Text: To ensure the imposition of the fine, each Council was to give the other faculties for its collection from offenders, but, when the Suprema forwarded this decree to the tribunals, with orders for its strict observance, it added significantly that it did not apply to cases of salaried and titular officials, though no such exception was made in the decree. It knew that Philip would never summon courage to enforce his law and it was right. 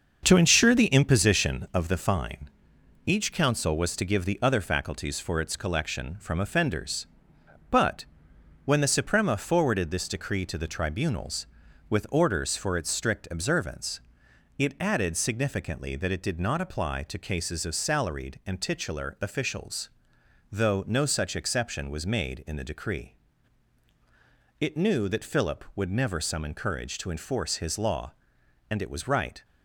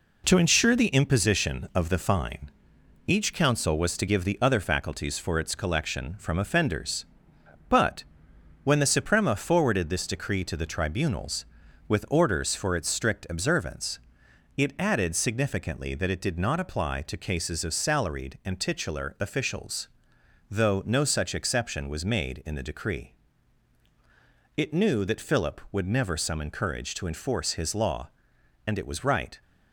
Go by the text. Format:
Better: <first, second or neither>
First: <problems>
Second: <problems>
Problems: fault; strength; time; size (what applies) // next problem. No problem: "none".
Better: second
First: starts louder than the rest; until 1.7 s; 6.5 dB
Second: none